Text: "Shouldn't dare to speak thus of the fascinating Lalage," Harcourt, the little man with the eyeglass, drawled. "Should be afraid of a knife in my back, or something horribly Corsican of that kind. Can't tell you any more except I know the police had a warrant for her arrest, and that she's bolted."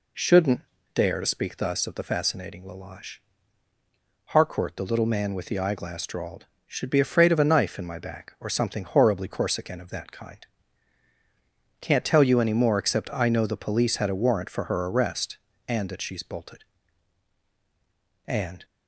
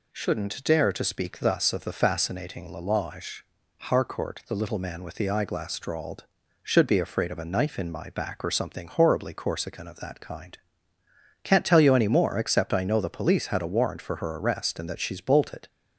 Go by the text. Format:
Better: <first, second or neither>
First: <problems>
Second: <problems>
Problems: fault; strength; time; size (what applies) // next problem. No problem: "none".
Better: second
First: pauses between "Shouldn't" and "dare"; slight; at 0.6 s; 0.32 s long // goes on to say "And"; slight; from 18.2 s on; 0.40 s long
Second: none